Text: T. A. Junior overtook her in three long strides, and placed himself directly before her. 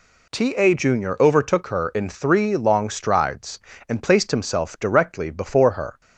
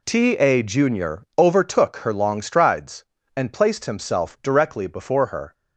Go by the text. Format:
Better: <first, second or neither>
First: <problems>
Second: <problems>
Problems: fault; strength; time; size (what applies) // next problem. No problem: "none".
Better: first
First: none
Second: pauses between "Junior" and "overtook"; slight; at 1.2 s; 0.16 s long // skips "in three"; at 2.1 s